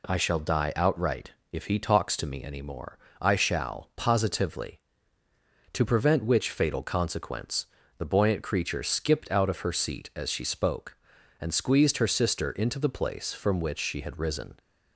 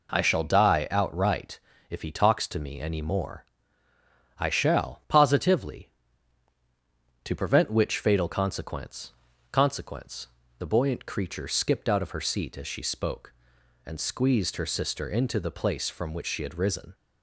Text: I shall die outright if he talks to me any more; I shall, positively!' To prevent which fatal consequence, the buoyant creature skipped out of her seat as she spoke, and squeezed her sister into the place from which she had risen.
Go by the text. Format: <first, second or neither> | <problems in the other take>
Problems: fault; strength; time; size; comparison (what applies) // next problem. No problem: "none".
first | pauses between "outright" and "if"; slight; at 1.6 s; 0.28 s long; slight in the first // says "consequence" twice; at 9.5 s